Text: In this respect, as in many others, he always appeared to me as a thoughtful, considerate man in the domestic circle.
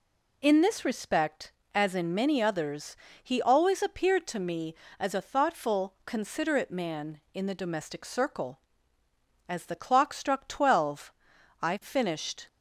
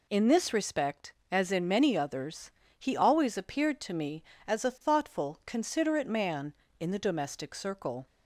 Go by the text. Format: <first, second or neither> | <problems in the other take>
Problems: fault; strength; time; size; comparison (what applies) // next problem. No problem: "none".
second | goes on to say "As the clock struck twelve I finished"; strong; from 9.4 s on; 2.9 s long